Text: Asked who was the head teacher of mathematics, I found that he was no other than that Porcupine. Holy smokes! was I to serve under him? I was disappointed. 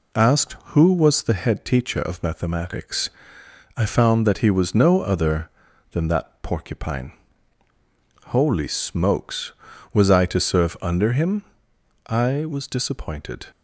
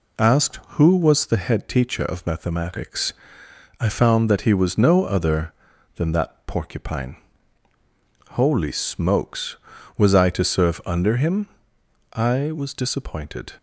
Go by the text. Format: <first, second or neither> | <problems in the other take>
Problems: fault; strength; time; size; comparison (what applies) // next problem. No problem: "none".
neither | none